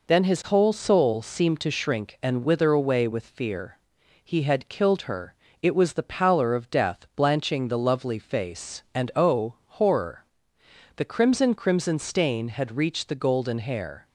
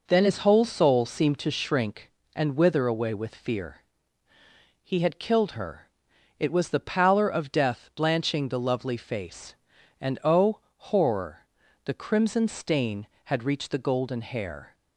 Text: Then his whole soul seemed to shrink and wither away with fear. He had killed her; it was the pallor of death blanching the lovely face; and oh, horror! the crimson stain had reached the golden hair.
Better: second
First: says "crimson" twice; at 11.5 s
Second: none

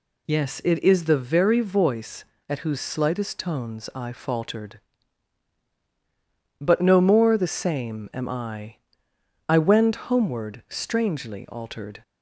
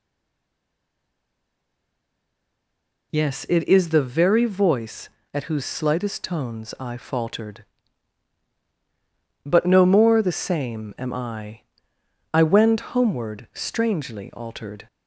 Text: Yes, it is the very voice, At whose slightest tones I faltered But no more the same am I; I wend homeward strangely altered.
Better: first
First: none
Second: stays silent before the first word; strong; until 3.1 s; 3.1 s long

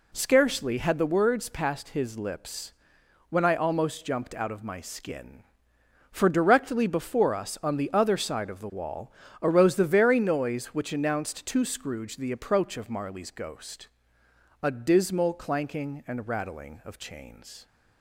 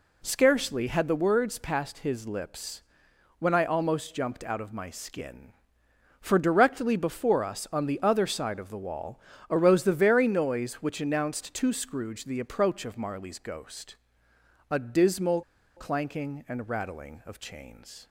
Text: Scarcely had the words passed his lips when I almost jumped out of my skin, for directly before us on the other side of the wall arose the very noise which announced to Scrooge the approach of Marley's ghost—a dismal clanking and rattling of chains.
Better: first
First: pauses between "lips" and "when"; noticeable; at 2.7 s; 0.56 s long // pauses between "wall" and "arose"; slight; at 9.1 s; 0.32 s long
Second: pauses between "lips" and "when"; noticeable; at 2.8 s; 0.56 s long // pauses between "wall" and "arose"; slight; at 9.1 s; 0.32 s long // pauses between "dismal" and "clanking"; slight; at 15.4 s; 0.35 s long

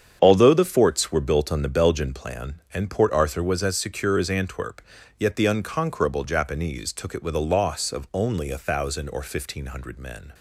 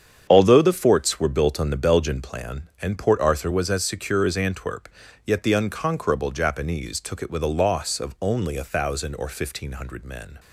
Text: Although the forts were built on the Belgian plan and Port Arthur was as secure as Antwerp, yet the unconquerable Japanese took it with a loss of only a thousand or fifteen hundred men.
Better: neither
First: starts louder than the rest; strong; until 1.2 s; 8 dB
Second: starts louder than the rest; strong; until 1.3 s; 8 dB

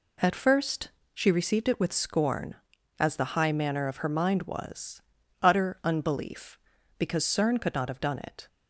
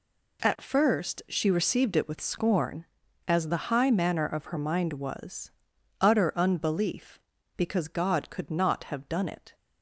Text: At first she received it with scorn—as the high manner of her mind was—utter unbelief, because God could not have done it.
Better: second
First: pauses between "first" and "she"; slight; at 0.8 s; 0.24 s long // says "Cern" for "God"; at 7.2 s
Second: none

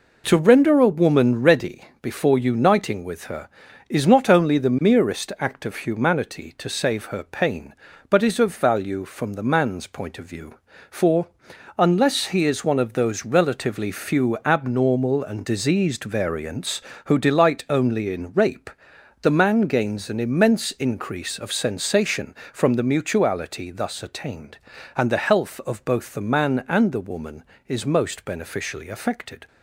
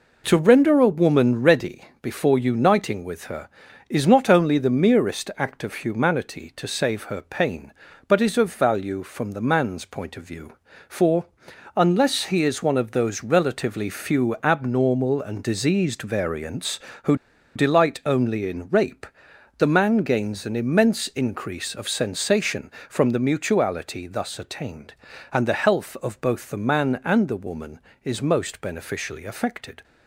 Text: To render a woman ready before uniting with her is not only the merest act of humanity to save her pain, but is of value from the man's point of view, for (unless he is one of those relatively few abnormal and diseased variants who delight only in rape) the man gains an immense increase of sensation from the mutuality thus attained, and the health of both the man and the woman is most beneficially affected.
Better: first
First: pauses between "ready" and "before"; slight; at 1.8 s; 0.18 s long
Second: pauses between "ready" and "before"; slight; at 1.8 s; 0.18 s long // pauses between "who" and "delight"; at 17.1 s; 0.40 s long

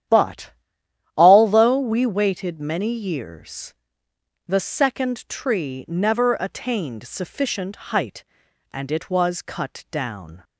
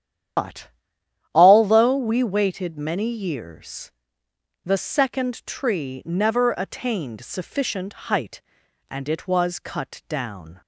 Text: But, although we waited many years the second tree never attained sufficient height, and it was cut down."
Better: first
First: starts louder than the rest; strong; until 1.7 s; 10.5 dB // pauses between "years" and "the"; noticeable; at 3.7 s; 0.72 s long // pauses between "sufficient" and "height"; slight; at 7.7 s; 0.16 s long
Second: loses the start of "But"; at 0.3 s; 100 ms // starts louder than the rest; strong; until 2.0 s; 10 dB // pauses between "years" and "the"; noticeable; at 3.9 s; 0.72 s long // pauses between "sufficient" and "height"; slight; at 7.9 s; 0.16 s long

